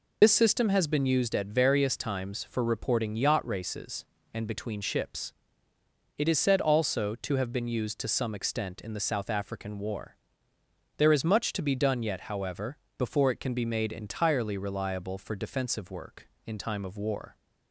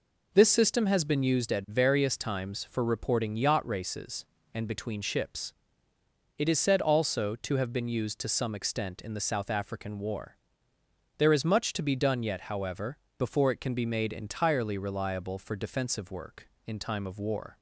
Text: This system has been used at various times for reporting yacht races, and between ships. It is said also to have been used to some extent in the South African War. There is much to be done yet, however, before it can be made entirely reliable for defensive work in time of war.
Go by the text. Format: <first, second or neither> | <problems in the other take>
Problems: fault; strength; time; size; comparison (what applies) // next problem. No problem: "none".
second | loses the start of "This"; at 0.2 s; 55 ms